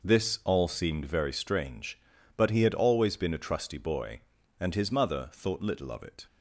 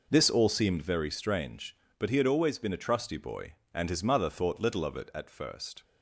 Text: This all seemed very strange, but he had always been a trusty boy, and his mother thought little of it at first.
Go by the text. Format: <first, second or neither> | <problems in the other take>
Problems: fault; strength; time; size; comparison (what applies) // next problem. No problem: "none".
second | stops before "at first"; at 6.2 s